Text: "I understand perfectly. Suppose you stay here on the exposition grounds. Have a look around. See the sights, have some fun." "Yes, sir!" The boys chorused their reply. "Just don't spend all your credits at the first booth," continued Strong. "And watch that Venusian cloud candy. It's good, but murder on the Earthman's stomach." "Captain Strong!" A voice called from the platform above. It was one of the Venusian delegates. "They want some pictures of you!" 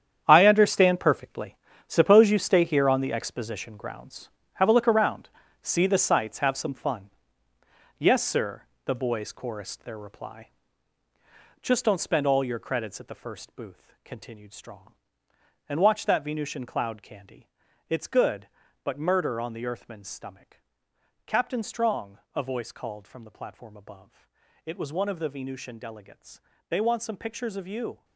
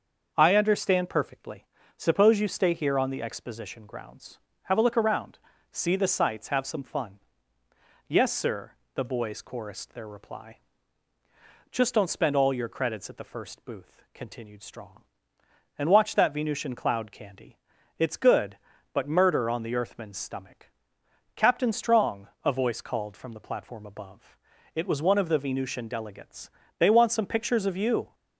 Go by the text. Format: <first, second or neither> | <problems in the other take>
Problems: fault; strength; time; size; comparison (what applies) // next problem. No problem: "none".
second | gets quieter; strong; throughout; 11.5 dB // starts louder than the rest; strong; until 1.2 s; 8.5 dB; also in the second